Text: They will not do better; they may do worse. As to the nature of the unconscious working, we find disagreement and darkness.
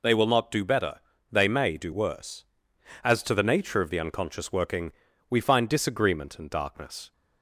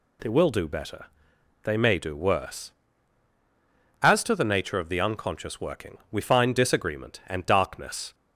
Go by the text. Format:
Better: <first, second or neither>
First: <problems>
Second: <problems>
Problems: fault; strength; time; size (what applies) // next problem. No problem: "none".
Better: first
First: none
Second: skips "not"; at 0.5 s